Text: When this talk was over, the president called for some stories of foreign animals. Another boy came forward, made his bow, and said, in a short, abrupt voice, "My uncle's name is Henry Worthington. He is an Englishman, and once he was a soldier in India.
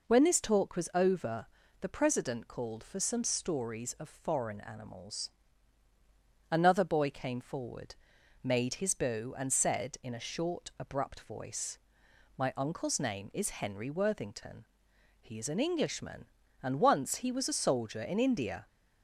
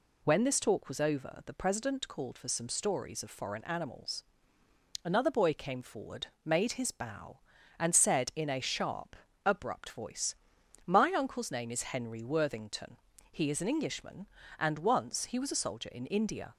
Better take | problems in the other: first | says "sharp" for "short"; at 8.5 s

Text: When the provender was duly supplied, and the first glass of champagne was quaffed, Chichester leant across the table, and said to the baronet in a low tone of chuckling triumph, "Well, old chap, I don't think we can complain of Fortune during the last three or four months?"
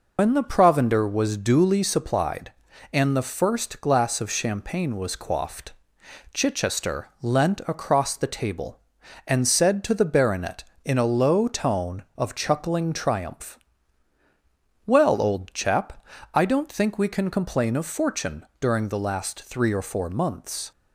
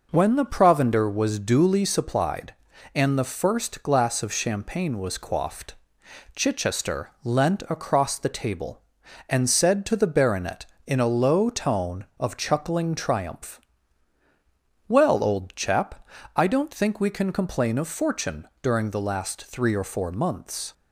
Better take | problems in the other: second | loses the start of "When"; at 0.1 s; 100 ms // pauses between "Fortune" and "during"; slight; at 18.4 s; 0.16 s long; slight in the second

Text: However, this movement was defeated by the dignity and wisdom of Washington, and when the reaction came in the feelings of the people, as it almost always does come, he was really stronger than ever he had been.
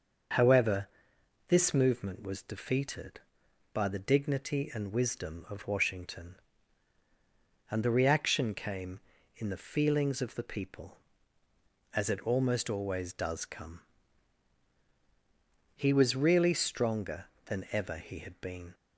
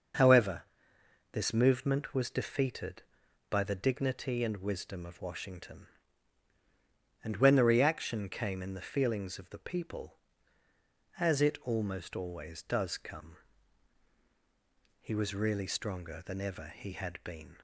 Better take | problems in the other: second | starts louder than the rest; until 1.9 s; 6.5 dB; noticeable in the second // skips "when"; at 7.8 s

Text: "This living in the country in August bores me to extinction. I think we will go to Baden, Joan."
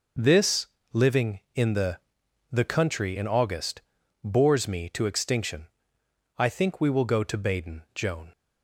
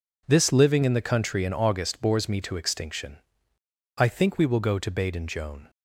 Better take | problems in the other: second | pauses between "This" and "living"; slight; at 0.6 s; 0.28 s long // says "the" twice; at 2.5 s // pauses between "August" and "bores"; at 3.8 s; 0.42 s long

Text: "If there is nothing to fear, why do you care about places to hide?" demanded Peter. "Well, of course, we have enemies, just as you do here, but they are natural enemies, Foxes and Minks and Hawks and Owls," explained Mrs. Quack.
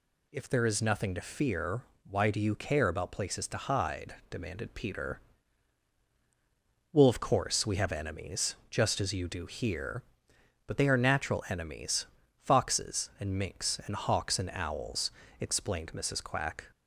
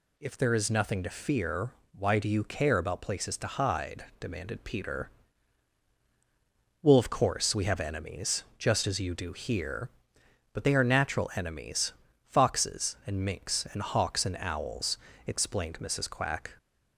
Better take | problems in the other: neither | none

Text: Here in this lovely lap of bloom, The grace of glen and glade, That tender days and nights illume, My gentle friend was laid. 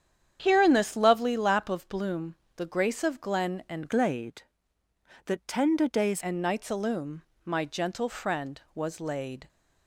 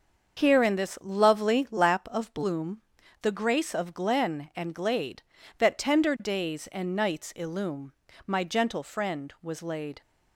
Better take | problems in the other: second | starts louder than the rest; strong; until 1.4 s; 8.5 dB; also in the second // changes voice from "glade" to "days"; from 3.8 to 6.2 s; 2.4 s long

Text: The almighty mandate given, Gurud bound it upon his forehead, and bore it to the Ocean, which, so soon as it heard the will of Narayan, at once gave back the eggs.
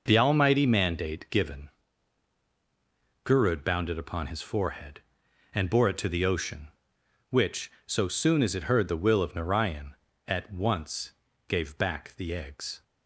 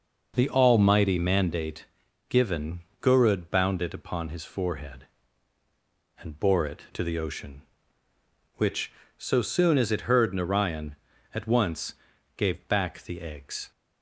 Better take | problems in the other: first | pauses between "mandate" and "given"; at 1.8 s; 0.44 s long // skips "the will of"; at 10.3 s // pauses between "once" and "gave"; at 11.9 s; 0.40 s long; also in the first

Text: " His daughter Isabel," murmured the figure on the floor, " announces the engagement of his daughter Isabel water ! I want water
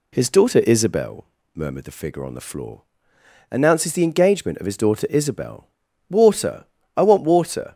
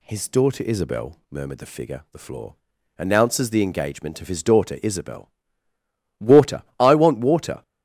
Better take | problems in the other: first | skips "on"; at 2.0 s // pauses between "Isabel" and "water"; noticeable; at 5.2 s; 0.96 s long; noticeable in the first

